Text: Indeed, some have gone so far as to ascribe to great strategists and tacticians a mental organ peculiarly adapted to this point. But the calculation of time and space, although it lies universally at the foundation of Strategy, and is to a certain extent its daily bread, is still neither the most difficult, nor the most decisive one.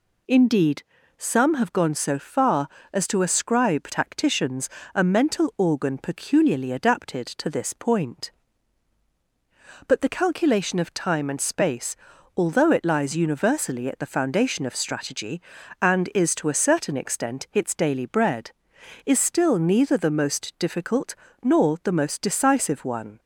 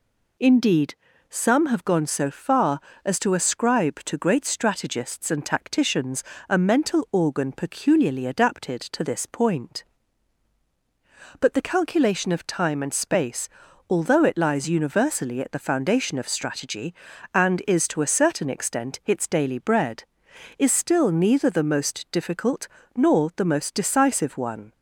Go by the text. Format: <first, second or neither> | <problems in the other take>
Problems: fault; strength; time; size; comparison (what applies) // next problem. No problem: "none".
second | skips "to great strategists and"; at 3.9 s // pauses between "tacticians" and "a"; slight; at 4.6 s; 0.24 s long; slight in the second